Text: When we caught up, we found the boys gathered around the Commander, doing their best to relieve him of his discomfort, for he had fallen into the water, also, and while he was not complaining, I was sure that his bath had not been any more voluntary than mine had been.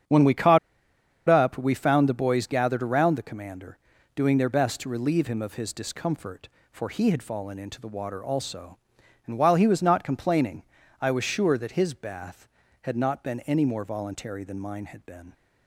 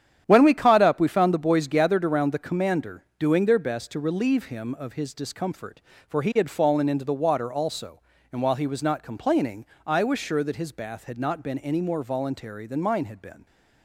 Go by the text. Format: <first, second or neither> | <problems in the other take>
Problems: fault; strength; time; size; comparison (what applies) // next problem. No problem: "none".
second | starts louder than the rest; strong; until 1.7 s; 8.5 dB; strong in the second // pauses between "caught" and "up"; noticeable; at 0.5 s; 0.70 s long